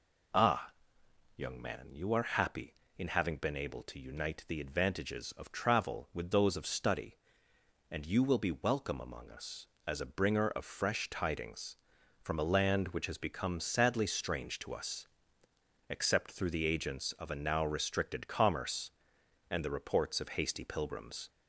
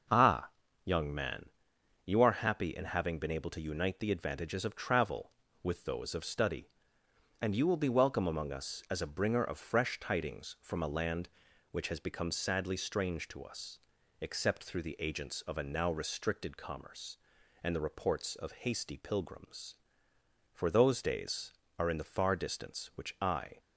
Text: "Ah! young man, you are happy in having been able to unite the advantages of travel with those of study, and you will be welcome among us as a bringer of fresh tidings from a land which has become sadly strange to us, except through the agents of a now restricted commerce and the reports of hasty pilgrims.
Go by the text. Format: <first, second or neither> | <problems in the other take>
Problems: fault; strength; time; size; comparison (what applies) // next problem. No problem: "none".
first | goes on to say "For those days are in the far distance which I"; strong; from 20.5 s on; 3.0 s long